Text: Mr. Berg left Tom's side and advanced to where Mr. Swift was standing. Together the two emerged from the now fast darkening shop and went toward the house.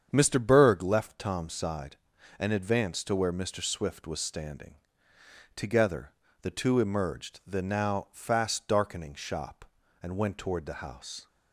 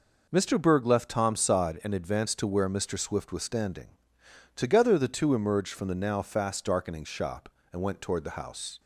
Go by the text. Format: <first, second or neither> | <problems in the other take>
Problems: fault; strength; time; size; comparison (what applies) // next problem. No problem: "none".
second | starts louder than the rest; strong; until 1.1 s; 7.5 dB // pauses between "Together" and "the"; slight; at 6.1 s; 0.28 s long // skips "from"; at 7.4 s